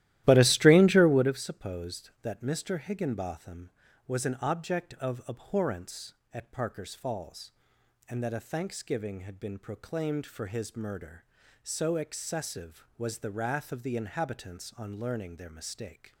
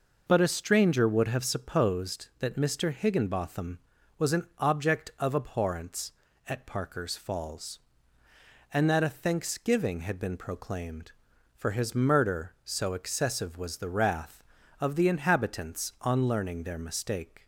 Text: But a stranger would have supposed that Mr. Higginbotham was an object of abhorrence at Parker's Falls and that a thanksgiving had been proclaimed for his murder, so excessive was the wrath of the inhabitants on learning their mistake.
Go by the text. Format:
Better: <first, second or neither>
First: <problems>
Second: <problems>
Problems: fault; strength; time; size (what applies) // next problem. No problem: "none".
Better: second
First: starts louder than the rest; strong; until 1.4 s; 14.5 dB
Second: none